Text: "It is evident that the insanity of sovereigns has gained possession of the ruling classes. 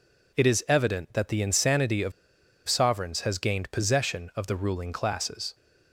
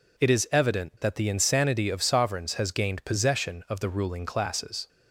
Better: second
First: pauses between "of" and "sovereigns"; noticeable; at 2.1 s; 0.56 s long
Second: none

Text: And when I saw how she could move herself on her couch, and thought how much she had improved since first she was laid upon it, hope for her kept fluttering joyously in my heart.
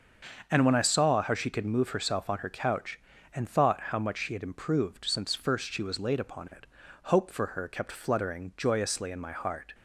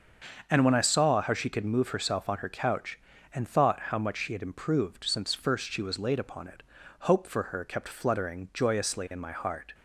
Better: neither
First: starts louder than the rest; until 1.5 s; 6.5 dB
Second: starts louder than the rest; until 1.4 s; 6.5 dB

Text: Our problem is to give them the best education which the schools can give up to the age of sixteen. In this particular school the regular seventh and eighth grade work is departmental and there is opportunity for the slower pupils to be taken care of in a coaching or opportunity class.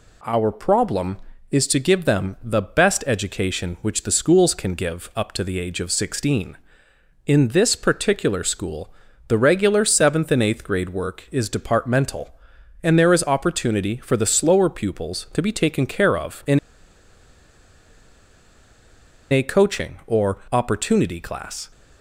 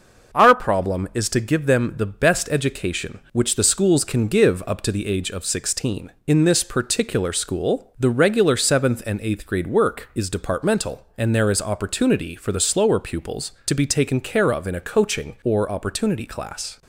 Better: second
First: pauses between "school" and "the"; slight; at 8.9 s; 0.36 s long // pauses between "in" and "a"; strong; at 16.5 s; 2.7 s long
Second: none

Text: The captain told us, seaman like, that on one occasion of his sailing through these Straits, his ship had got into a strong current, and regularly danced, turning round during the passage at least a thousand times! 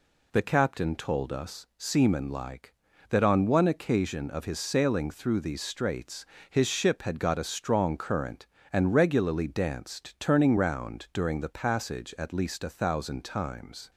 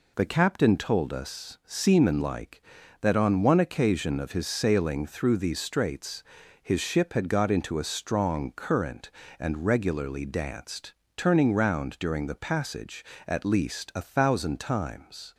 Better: second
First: skips "into"; at 7.3 s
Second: none

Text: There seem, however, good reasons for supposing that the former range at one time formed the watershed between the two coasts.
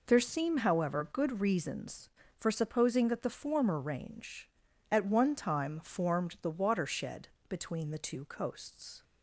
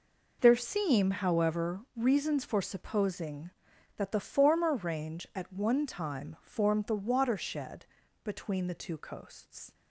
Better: first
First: pauses between "watershed" and "between"; slight; at 7.2 s; 0.20 s long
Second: skips "good"; at 1.8 s // pauses between "watershed" and "between"; at 7.8 s; 0.38 s long

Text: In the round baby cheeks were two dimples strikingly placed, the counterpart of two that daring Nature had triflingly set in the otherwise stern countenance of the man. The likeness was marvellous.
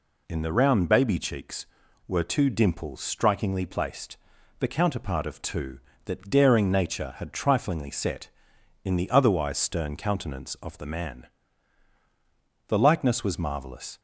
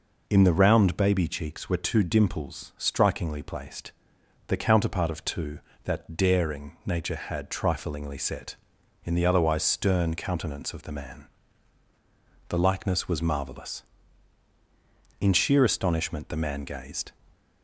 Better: first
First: none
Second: goes on to say "In sheer astonishment the man gazed"; strong; from 15.1 s on; 1.9 s long

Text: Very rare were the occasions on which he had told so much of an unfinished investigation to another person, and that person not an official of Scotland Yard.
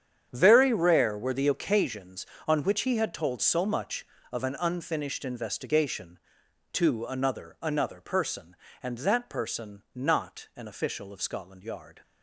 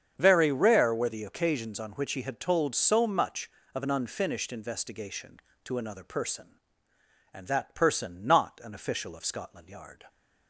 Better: second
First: starts louder than the rest; strong; until 1.3 s; 8.5 dB // says "another" twice; at 7.6 s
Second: starts louder than the rest; strong; until 1.1 s; 7.5 dB

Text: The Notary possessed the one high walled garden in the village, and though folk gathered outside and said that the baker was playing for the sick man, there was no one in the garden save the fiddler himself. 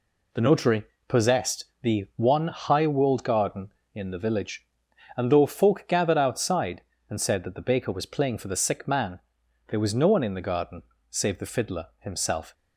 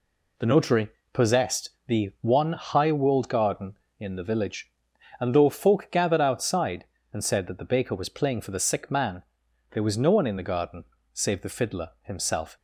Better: neither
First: pauses between "Notary" and "possessed"; slight; at 0.8 s; 0.24 s long // pauses between "possessed" and "the"; slight; at 1.6 s; 0.18 s long // pauses between "garden" and "save"; slight; at 10.8 s; 0.26 s long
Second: pauses between "Notary" and "possessed"; slight; at 0.8 s; 0.24 s long // pauses between "possessed" and "the"; slight; at 1.6 s; 0.18 s long // pauses between "garden" and "save"; slight; at 10.8 s; 0.28 s long

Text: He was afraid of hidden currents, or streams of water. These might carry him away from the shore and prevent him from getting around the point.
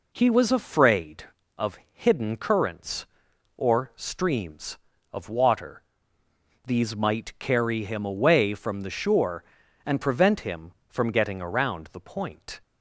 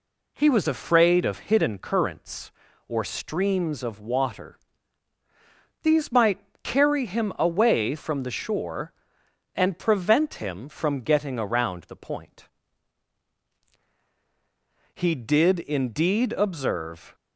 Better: first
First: none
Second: pauses between "might" and "carry"; slight; at 6.4 s; 0.22 s long // goes on to say "He did indeed observe"; strong; from 14.9 s on; 2.2 s long

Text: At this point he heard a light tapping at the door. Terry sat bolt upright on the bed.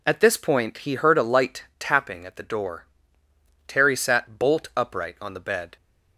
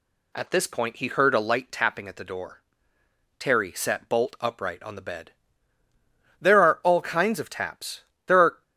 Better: first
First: none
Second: goes on to say "There are all kinds of taps There are"; strong; from 6.4 s on; 2.2 s long

